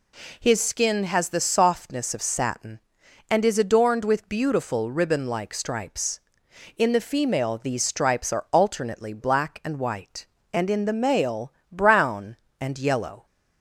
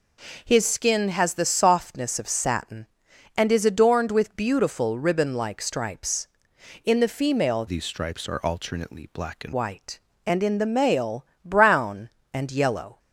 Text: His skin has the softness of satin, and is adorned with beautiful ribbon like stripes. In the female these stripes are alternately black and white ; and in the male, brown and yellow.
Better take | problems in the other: first | changes voice from "these" to "and"; from 7.6 to 9.5 s; 1.9 s long

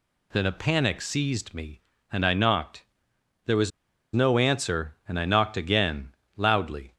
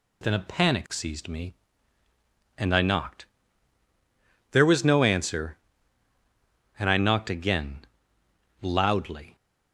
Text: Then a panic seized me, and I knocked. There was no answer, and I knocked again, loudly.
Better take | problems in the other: second | pauses between "was" and "no"; at 3.7 s; 0.43 s long

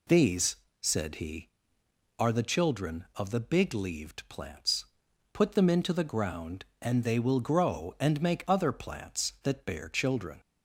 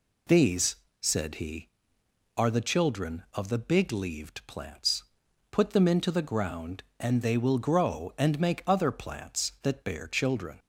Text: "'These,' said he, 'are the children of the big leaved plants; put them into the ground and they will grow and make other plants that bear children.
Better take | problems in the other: neither | none

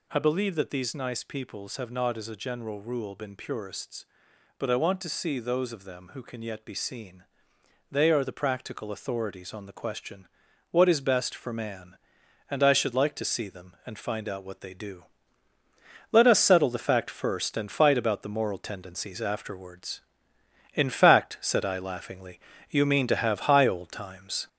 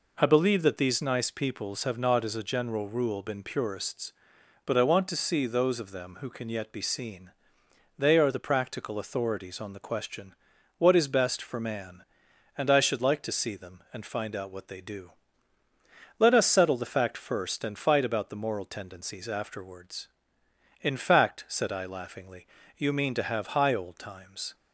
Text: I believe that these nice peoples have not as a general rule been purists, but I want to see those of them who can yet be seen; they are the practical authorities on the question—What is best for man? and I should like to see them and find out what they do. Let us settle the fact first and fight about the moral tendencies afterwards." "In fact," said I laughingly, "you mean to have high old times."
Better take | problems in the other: second | gets louder; noticeable; throughout; 4.5 dB

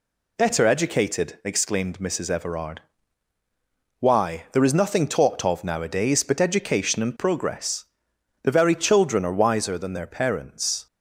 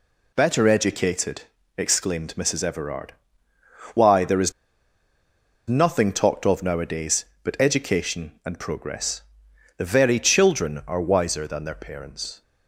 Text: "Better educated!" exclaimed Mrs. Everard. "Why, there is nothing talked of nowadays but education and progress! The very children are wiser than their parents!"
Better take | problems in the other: first | pauses between "is" and "nothing"; at 4.5 s; 1.1 s long

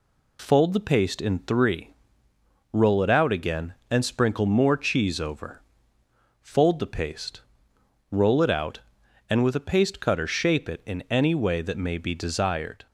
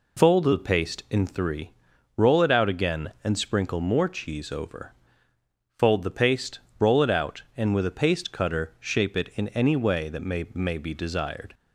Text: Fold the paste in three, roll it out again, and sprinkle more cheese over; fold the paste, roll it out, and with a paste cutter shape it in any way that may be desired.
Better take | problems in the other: first | says "may" twice; at 10.5 s

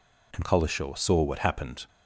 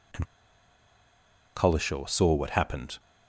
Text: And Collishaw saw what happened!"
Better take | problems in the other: first | pauses between "And" and "Collishaw"; strong; at 0.2 s; 1.3 s long

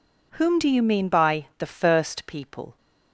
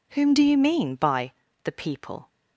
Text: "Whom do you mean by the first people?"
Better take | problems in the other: first | pauses between "by" and "the"; slight; at 1.3 s; 0.32 s long // skips "first"; at 1.7 s

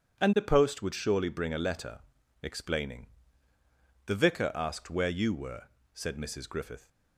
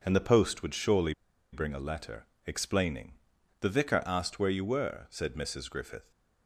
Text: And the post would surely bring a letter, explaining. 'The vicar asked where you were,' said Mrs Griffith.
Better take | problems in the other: first | pauses between "surely" and "bring"; at 1.1 s; 0.40 s long

